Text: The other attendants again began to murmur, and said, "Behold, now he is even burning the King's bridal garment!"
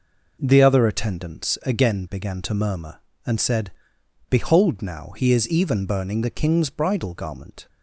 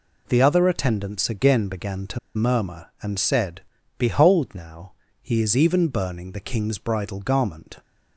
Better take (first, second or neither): first